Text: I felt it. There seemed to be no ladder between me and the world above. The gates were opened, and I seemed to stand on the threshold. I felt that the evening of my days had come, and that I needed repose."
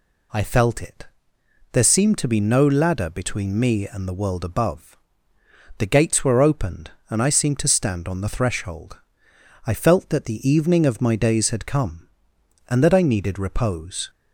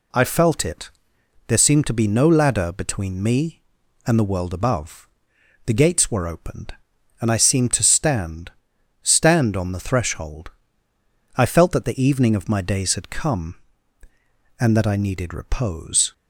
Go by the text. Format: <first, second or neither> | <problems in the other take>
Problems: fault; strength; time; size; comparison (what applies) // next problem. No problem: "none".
first | says "stand" twice; at 9.0 s